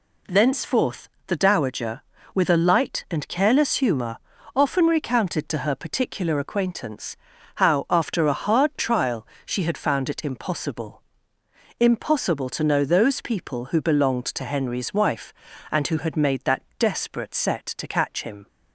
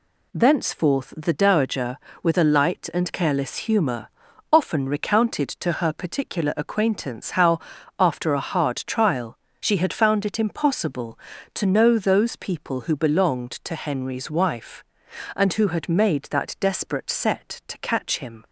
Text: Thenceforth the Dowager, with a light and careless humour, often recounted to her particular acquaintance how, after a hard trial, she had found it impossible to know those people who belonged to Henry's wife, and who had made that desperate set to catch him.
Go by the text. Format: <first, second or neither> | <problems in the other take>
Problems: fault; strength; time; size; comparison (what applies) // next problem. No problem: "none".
second | pauses between "Thenceforth" and "the"; slight; at 1.0 s; 0.20 s long // pauses between "acquaintance" and "how"; at 7.1 s; 0.40 s long // says "impossible" twice; at 11.7 s // pauses between "that" and "desperate"; slight; at 16.6 s; 0.16 s long